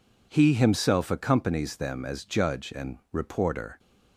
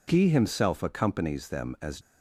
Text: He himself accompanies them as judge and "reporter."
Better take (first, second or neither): first